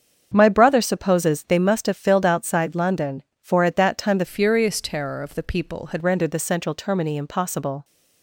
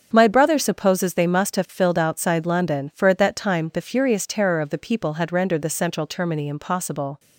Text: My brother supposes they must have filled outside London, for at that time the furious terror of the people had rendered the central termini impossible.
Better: second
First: starts louder than the rest; strong; until 1.3 s; 7 dB // changes voice from "furious" to "had"; from 4.2 to 6.0 s; 1.8 s long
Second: starts louder than the rest; strong; until 1.1 s; 7 dB

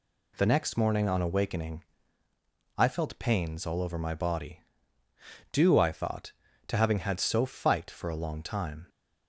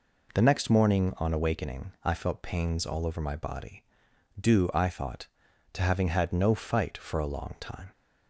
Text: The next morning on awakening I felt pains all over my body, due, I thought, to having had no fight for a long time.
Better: second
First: pauses between "awakening" and "I"; noticeable; at 1.8 s; 0.92 s long // says "so" for "no"; at 7.2 s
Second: none

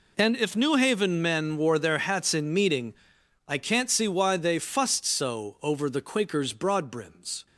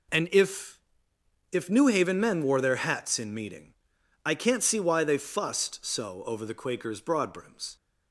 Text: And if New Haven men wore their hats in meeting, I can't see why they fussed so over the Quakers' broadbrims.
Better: first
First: none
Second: says "if" twice; at 1.5 s

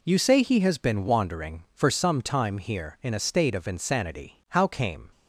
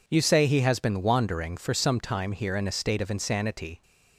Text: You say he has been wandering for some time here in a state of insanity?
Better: second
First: goes on to say "How came"; noticeable; from 4.4 s on; 0.62 s long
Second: none

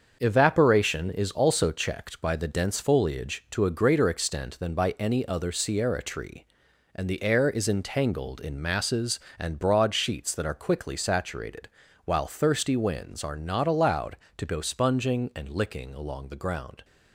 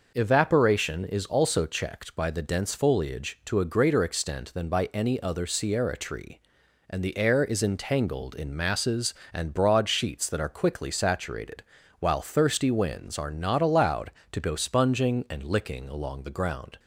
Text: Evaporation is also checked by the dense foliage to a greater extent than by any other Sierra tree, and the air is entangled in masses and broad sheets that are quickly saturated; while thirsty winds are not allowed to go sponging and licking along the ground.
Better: second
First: gets quieter; throughout; 6.5 dB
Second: none

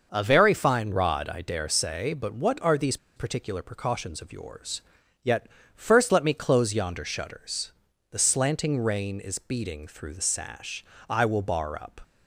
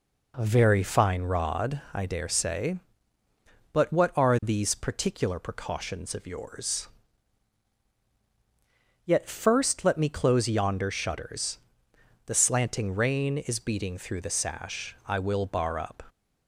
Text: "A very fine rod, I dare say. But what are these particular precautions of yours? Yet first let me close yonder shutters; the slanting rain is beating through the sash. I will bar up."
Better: second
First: starts louder than the rest; noticeable; until 1.1 s; 6 dB // pauses between "these" and "particular"; slight; at 2.9 s; 0.19 s long // pauses between "Yet" and "first"; slight; at 5.4 s; 0.26 s long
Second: none

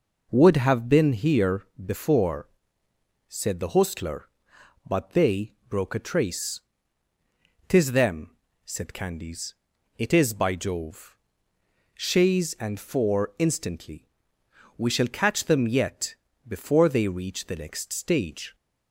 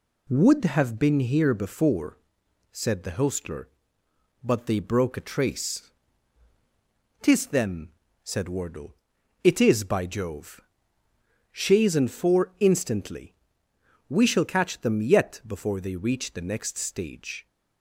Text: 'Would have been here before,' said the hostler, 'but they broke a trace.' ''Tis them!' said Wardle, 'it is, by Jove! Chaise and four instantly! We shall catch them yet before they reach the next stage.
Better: second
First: pauses between "here" and "before"; slight; at 1.6 s; 0.18 s long // pauses between "they" and "broke"; slight; at 5.5 s; 0.16 s long // says "Candies" for "Wardle"; at 8.9 s // pauses between "yet" and "before"; slight; at 16.1 s; 0.32 s long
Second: none

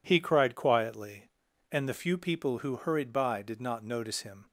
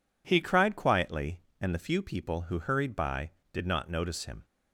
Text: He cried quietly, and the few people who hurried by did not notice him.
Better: first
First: none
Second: changes voice at "cried"; from 0.4 s on; 4.0 s long

